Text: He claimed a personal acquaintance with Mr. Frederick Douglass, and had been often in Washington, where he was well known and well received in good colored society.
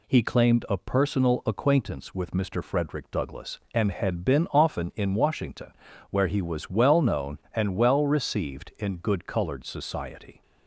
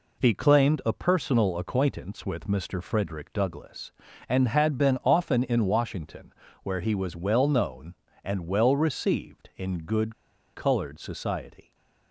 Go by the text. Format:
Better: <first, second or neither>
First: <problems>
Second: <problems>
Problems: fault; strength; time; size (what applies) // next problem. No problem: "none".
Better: first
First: none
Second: pauses between "good" and "colored"; at 10.1 s; 0.41 s long